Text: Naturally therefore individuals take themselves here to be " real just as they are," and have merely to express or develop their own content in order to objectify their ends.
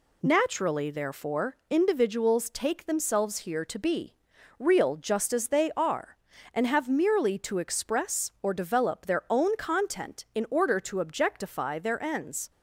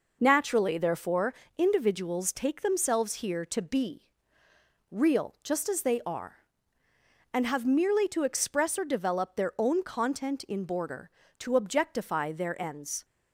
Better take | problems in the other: first | pauses between "therefore" and "individuals"; slight; at 1.3 s; 0.24 s long // says "border" for "order"; at 10.6 s

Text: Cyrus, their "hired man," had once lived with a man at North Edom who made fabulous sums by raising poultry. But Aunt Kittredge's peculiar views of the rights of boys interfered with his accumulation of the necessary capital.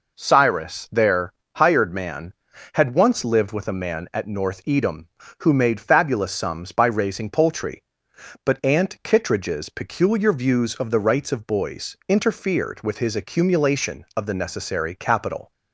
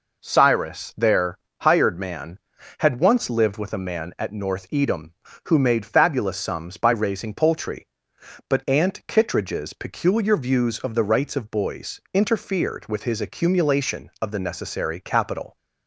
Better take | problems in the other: neither | pauses between "their" and "hired"; slight; the same in both

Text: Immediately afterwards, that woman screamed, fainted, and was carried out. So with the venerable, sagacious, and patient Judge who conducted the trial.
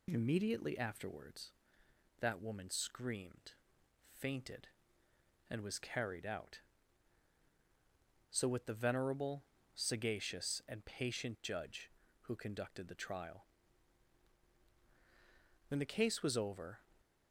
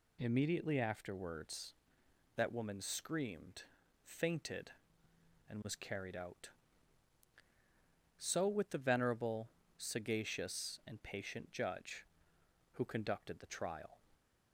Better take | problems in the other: second | goes on to say "When the case was over"; noticeable; from 15.6 s on; 1.1 s long

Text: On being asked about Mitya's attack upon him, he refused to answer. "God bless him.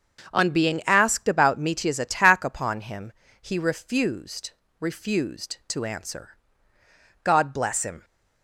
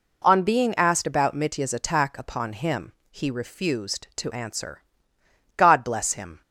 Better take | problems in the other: second | starts louder than the rest; until 1.3 s; 6.5 dB // says "refused" twice; at 4.8 s

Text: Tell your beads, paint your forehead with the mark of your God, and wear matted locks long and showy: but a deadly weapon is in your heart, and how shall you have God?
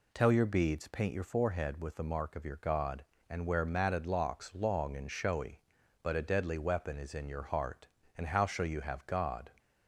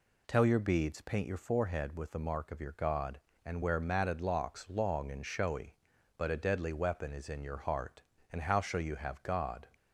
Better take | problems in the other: neither | none

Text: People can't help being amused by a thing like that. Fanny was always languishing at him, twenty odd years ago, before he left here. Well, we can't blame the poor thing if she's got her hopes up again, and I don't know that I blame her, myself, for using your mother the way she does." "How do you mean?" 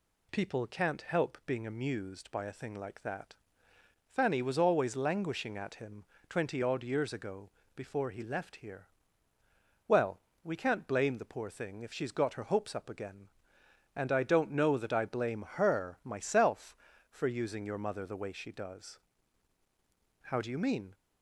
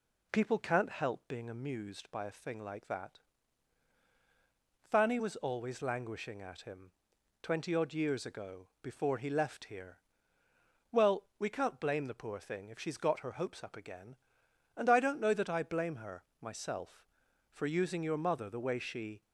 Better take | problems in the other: first | stops before "does How do you mean"; at 19.2 s

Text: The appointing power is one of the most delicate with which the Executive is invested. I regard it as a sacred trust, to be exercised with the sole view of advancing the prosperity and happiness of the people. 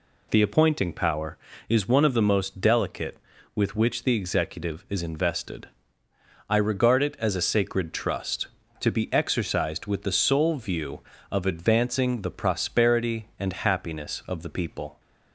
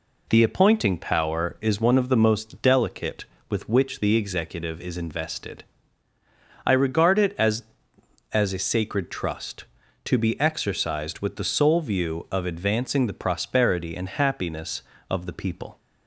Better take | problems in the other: first | says "as" twice; at 8.3 s

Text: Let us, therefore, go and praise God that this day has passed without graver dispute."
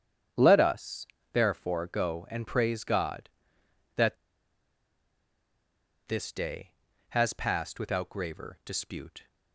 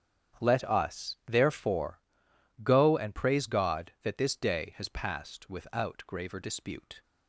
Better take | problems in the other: second | starts louder than the rest; strong; until 1.6 s; 8.5 dB; strong in the second // pauses between "that" and "this"; strong; at 4.1 s; 1.9 s long

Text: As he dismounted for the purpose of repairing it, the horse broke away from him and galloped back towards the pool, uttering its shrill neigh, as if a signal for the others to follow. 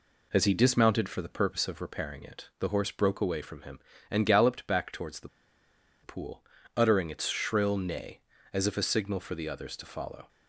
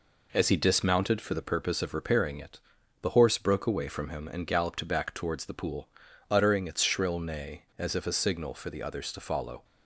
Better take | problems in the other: second | pauses between "the" and "pool"; noticeable; at 5.2 s; 0.74 s long

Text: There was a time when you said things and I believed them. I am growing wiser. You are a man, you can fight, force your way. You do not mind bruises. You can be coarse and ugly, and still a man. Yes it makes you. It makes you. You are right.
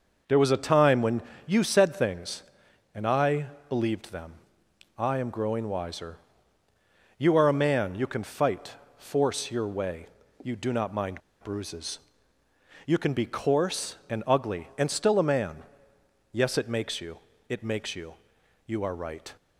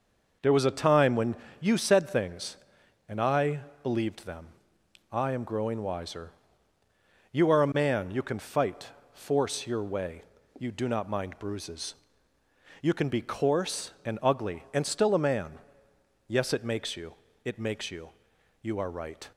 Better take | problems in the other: second | pauses between "when" and "you"; slight; at 1.2 s; 0.24 s long; slight in the second // pauses between "I" and "believed"; slight; at 3.4 s; 0.22 s long; slight in the second // pauses between "mind" and "bruises"; slight; at 11.2 s; 0.22 s long

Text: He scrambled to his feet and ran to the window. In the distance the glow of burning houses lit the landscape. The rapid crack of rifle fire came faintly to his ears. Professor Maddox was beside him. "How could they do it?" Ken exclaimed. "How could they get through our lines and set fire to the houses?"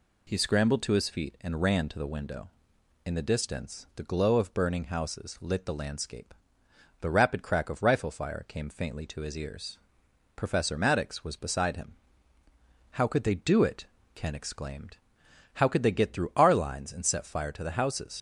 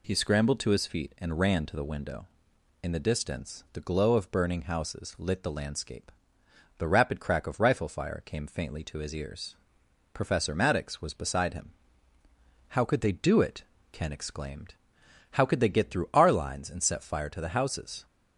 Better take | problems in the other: second | leaves "houses" unfinished; at 18.1 s; 80 ms

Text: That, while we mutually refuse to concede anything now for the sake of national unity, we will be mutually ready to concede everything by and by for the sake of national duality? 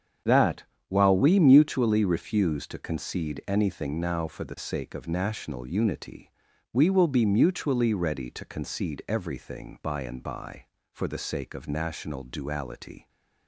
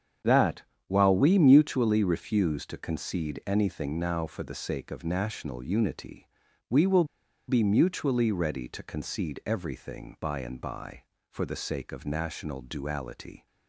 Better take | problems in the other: first | starts louder than the rest; strong; until 1.5 s; 8 dB; strong in the first // pauses between "will" and "be"; at 7.0 s; 0.43 s long

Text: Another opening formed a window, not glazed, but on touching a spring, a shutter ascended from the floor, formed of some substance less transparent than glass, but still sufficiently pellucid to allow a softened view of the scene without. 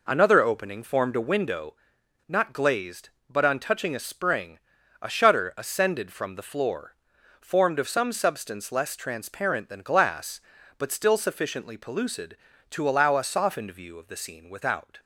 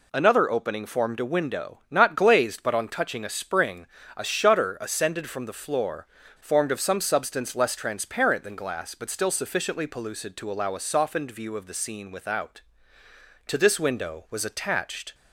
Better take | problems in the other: first | goes on to say "To this window was attached"; strong; from 13.4 s on; 1.6 s long

